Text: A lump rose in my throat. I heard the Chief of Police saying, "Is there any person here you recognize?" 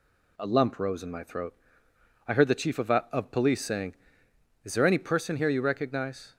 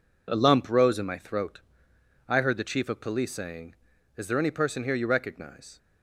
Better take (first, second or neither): second